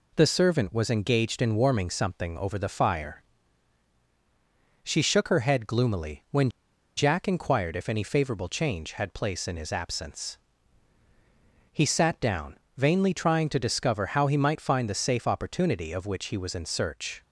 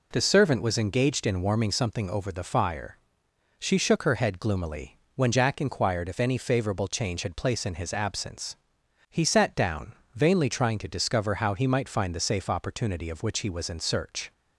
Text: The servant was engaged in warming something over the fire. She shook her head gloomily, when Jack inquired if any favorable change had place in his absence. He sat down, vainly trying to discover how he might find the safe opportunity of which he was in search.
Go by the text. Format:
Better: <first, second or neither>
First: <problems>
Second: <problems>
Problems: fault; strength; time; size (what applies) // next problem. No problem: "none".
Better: second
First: pauses between "when" and "Jack"; noticeable; at 6.5 s; 0.46 s long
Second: none